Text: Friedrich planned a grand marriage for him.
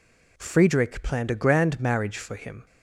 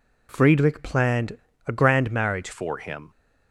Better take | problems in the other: first | pauses between "planned" and "a"; slight; at 1.3 s; 0.30 s long // changes voice at "for"; from 2.5 s on; 0.5 s long

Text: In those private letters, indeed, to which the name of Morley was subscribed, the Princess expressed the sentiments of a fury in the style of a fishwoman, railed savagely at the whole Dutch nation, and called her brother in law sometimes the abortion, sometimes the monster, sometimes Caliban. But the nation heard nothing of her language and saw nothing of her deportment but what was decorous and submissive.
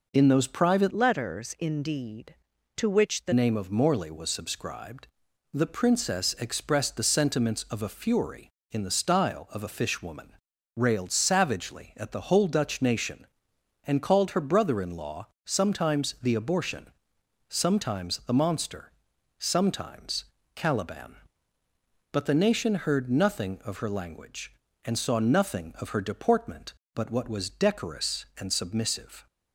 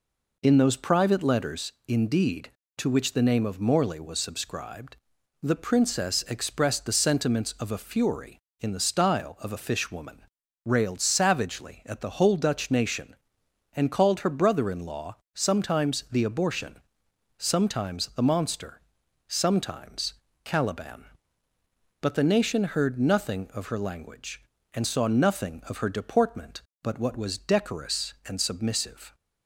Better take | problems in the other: second | changes voice from "letters" to "the"; from 0.9 to 3.3 s; 2.4 s long // pauses between "law" and "sometimes"; slight; at 15.2 s; 0.18 s long; slight in the second // pauses between "sometimes" and "Caliban"; slight; at 20.2 s; 0.30 s long; slight in the second

